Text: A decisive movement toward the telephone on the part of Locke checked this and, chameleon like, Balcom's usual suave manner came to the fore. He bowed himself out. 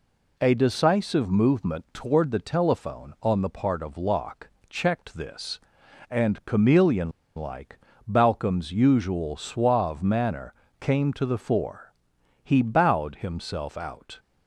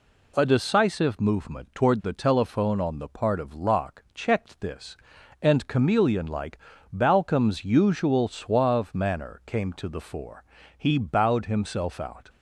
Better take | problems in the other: second | pauses between "Locke" and "checked"; slight; at 4.4 s; 0.20 s long // pauses between "chameleon" and "like"; slight; at 7.1 s; 0.25 s long // pauses between "manner" and "came"; slight; at 10.5 s; 0.26 s long

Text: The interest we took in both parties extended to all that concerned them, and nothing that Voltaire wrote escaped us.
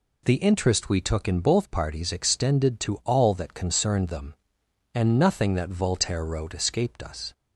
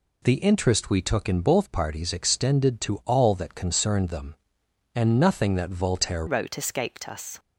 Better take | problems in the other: first | changes voice at "wrote"; from 6.2 s on; 1.1 s long

